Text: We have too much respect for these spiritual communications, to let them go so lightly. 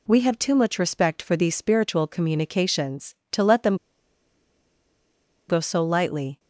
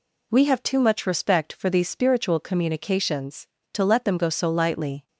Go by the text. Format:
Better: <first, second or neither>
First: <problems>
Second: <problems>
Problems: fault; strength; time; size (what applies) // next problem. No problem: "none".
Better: second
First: pauses between "them" and "go"; strong; at 3.7 s; 1.7 s long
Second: none